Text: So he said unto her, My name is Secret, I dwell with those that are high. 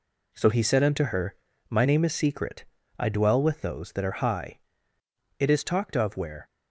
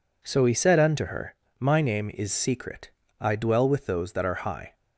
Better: second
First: goes on to say "It is talked of where"; noticeable; from 5.4 s on; 1.0 s long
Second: none

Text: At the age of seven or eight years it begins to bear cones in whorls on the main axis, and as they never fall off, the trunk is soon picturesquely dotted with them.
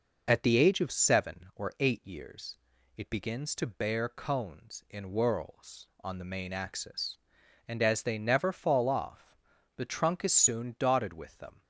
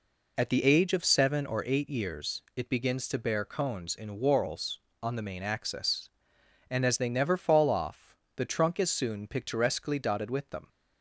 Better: second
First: pauses between "years" and "it"; at 2.5 s; 0.38 s long // skips "picturesquely"; at 10.7 s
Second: pauses between "years" and "it"; slight; at 2.4 s; 0.16 s long

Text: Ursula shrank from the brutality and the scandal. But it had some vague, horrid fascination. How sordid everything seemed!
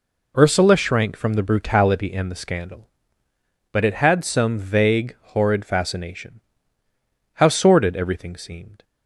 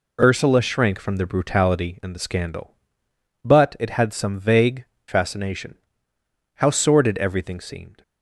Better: first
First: none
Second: skips "horrid"; at 4.9 s

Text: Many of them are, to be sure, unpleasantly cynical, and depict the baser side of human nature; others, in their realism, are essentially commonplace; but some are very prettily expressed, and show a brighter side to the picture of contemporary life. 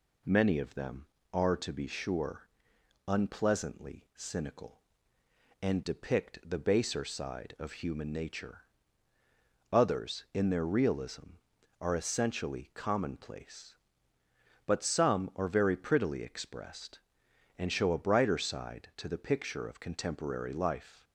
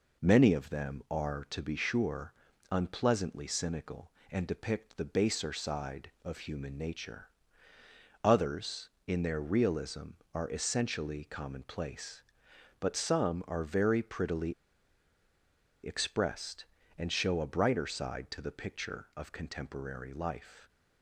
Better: first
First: none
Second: pauses between "prettily" and "expressed"; strong; at 14.5 s; 1.3 s long

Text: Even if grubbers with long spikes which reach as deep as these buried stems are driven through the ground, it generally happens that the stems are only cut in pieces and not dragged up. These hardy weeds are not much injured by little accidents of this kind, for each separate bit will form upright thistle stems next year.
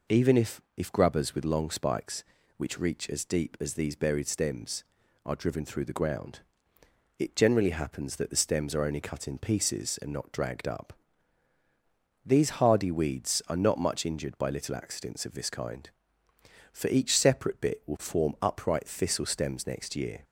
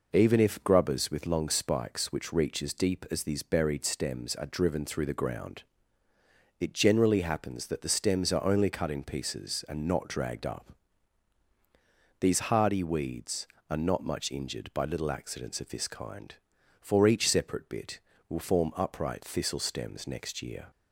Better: second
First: says "if" twice; at 0.7 s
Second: none

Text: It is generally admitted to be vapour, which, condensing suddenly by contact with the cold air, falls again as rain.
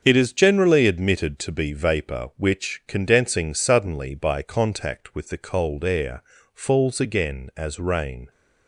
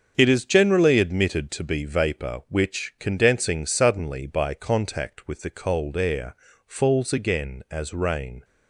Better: neither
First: starts louder than the rest; until 1.0 s; 7 dB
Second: starts louder than the rest; until 1.1 s; 7 dB

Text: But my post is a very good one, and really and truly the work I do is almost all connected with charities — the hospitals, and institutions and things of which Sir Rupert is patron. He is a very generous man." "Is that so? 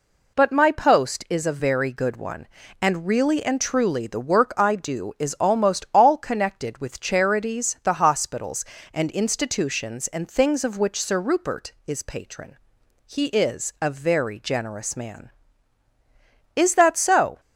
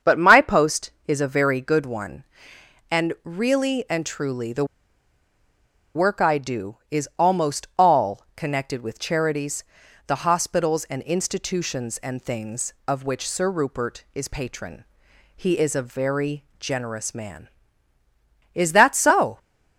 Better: first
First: none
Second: starts louder than the rest; strong; until 1.2 s; 7.5 dB // pauses between "the" and "work"; strong; at 4.6 s; 1.3 s long

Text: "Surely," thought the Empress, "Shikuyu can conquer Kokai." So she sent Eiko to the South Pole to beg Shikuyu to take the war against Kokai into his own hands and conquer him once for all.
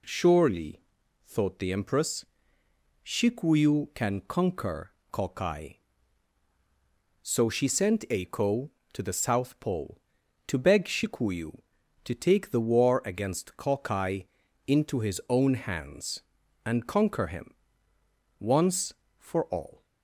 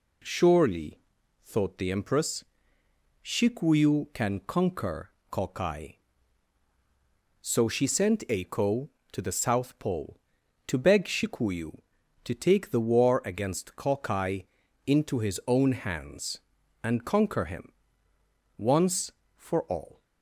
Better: neither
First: pauses between "conquer" and "Kokai"; slight; at 4.9 s; 0.20 s long // pauses between "Kokai" and "into"; at 14.2 s; 0.40 s long // pauses between "him" and "once"; noticeable; at 17.5 s; 0.86 s long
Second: pauses between "conquer" and "Kokai"; slight; at 5.1 s; 0.20 s long // pauses between "Kokai" and "into"; at 14.4 s; 0.40 s long // pauses between "him" and "once"; noticeable; at 17.7 s; 0.86 s long

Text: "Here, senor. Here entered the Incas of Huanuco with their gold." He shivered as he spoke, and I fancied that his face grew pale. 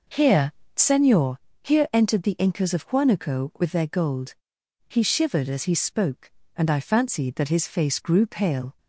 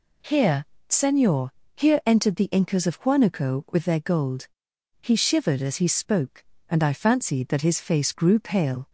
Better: second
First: starts louder than the rest; noticeable; until 1.3 s; 5.5 dB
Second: none

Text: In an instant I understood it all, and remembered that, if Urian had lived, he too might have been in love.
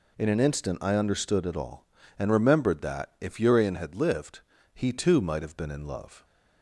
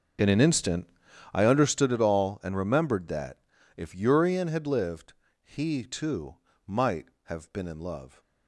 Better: first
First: none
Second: starts louder than the rest; noticeable; until 1.9 s; 6 dB // pauses between "instant" and "I"; noticeable; at 0.8 s; 0.46 s long // pauses between "too" and "might"; slight; at 6.3 s; 0.30 s long

